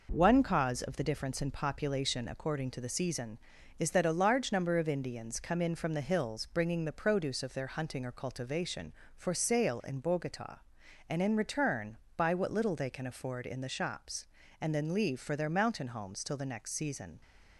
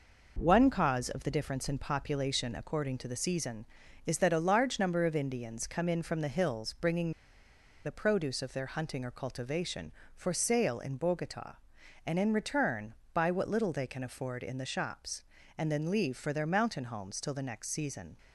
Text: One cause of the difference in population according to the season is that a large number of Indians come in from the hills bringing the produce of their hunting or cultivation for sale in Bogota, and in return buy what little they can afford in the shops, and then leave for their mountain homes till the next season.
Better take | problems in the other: first | pauses between "bringing" and "the"; noticeable; at 7.1 s; 0.73 s long // pauses between "return" and "buy"; slight; at 12.9 s; 0.18 s long; slight in the first

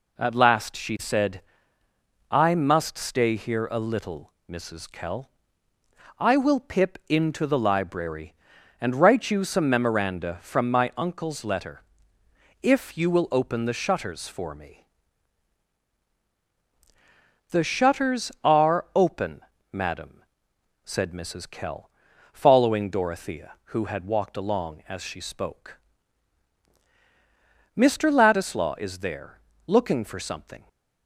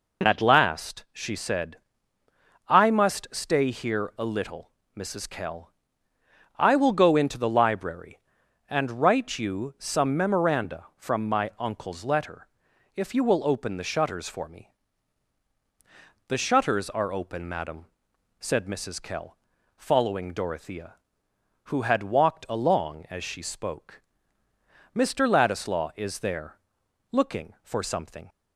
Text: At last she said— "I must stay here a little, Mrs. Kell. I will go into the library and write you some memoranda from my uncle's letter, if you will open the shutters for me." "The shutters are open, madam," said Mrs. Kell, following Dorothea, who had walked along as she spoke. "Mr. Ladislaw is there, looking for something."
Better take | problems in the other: second | says "pip" for "go"; at 6.5 s

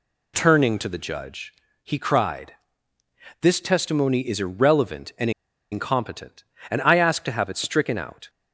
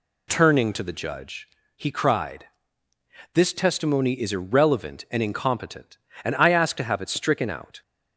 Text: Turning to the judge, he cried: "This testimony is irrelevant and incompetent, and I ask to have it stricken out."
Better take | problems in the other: second | pauses between "and" and "incompetent"; at 5.3 s; 0.41 s long

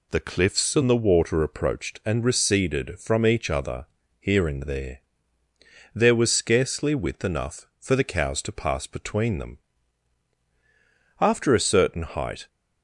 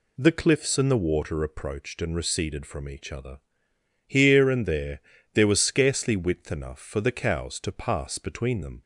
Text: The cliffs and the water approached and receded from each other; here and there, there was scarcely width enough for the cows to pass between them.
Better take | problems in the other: second | goes on to say "After a certain height"; noticeable; from 11.1 s on; 1.2 s long

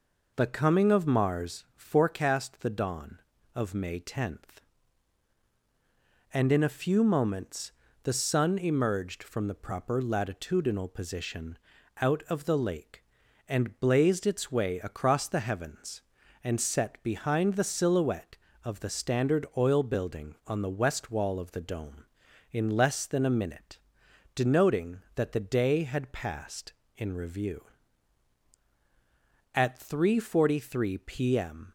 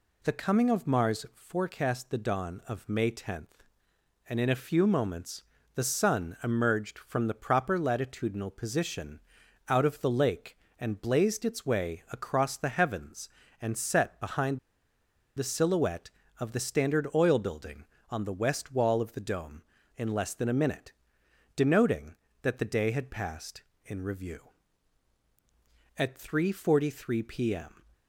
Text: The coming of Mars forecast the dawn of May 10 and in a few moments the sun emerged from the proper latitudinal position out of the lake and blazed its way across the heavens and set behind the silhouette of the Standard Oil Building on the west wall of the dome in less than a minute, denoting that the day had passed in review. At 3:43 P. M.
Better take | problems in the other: first | pauses between "moments" and "the"; slight; at 5.4 s; 0.32 s long; slight in the first // pauses between "position" and "out"; noticeable; at 9.1 s; 0.50 s long; also in the first // pauses between "behind" and "the"; noticeable; at 14.5 s; 0.78 s long

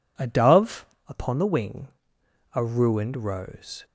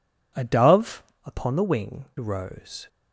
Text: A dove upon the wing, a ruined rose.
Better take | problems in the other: first | pauses between "dove" and "upon"; slight; at 1.0 s; 0.22 s long; slight in the first // skips "a ruined"; at 2.1 s

